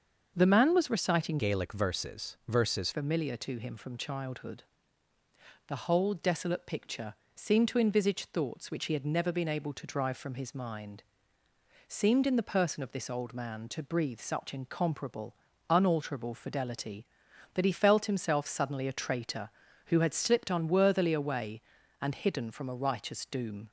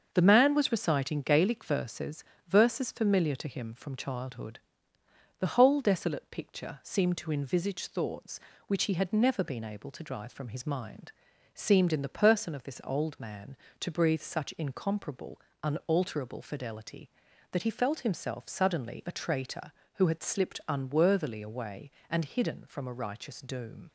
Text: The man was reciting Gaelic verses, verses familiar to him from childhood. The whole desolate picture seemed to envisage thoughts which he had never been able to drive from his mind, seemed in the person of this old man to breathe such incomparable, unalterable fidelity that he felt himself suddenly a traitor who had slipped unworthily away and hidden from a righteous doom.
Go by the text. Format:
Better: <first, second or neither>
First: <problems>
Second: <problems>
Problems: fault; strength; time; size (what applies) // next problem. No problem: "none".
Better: second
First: starts louder than the rest; until 1.3 s; 6.5 dB // changes voice from "Gaelic" to "verses"; from 1.3 to 2.8 s; 1.5 s long // pauses between "picture" and "seemed"; slight; at 7.1 s; 0.20 s long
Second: starts louder than the rest; until 1.1 s; 6.5 dB